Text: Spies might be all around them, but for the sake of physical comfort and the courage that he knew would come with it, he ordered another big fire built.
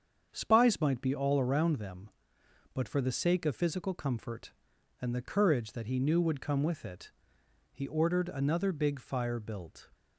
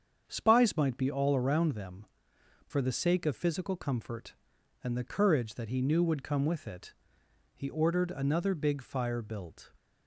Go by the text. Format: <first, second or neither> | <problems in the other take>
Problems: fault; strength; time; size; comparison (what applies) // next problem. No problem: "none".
first | starts louder than the rest; strong; until 1.2 s; 7.5 dB; strong in the first // skips "but"; at 2.3 s